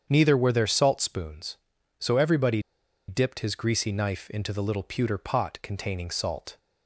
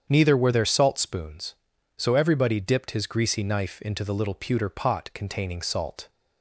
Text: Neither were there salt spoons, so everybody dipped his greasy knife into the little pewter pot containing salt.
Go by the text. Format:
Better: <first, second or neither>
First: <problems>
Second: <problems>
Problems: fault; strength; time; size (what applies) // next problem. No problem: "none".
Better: second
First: starts louder than the rest; strong; until 1.1 s; 8 dB // pauses between "everybody" and "dipped"; noticeable; at 2.6 s; 0.46 s long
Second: starts louder than the rest; strong; until 1.1 s; 8 dB